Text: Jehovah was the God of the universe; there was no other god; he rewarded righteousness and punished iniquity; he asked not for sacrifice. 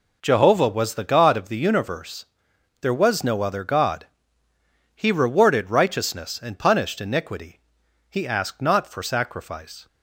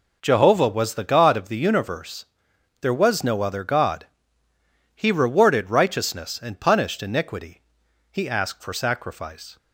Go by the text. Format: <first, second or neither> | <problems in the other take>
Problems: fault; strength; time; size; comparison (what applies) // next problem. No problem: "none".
first | skips "not"; at 8.6 s